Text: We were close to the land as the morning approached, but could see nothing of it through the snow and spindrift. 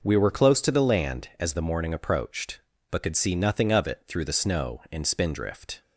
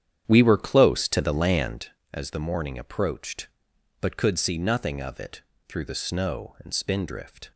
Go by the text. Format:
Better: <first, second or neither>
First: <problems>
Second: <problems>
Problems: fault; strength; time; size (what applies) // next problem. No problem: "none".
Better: first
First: none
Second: starts louder than the rest; strong; until 1.8 s; 9.5 dB // pauses between "it" and "through"; slight; at 5.4 s; 0.26 s long